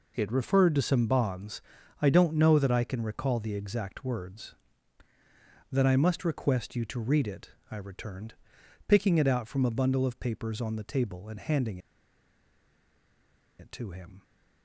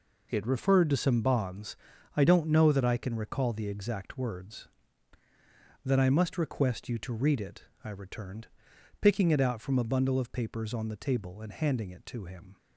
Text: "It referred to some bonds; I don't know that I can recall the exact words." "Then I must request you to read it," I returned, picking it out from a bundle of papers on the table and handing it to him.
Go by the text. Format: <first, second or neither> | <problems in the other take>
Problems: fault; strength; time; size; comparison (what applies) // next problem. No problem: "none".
second | pauses between "handing" and "it"; strong; at 11.7 s; 1.8 s long